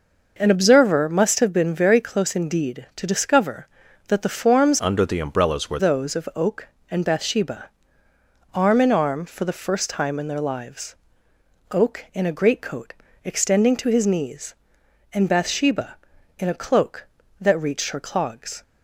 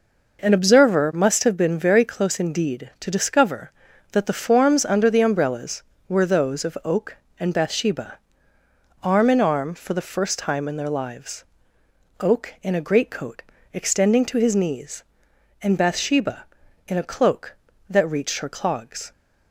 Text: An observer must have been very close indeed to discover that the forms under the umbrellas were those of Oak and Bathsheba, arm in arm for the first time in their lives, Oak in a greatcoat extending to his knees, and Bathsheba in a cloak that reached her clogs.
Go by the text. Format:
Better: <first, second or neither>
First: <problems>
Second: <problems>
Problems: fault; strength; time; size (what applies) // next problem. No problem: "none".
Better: second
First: changes voice from "under" to "were"; from 4.7 to 5.7 s; 1.0 s long // pauses between "greatcoat" and "extending"; slight; at 12.9 s; 0.28 s long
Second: pauses between "greatcoat" and "extending"; slight; at 13.4 s; 0.28 s long